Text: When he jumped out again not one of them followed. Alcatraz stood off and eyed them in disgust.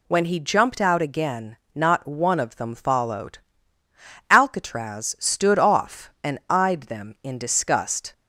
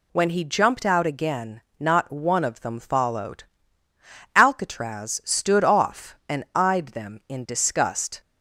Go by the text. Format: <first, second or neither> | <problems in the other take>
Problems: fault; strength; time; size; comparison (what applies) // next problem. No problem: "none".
neither | pauses between "again" and "not"; slight; the same in both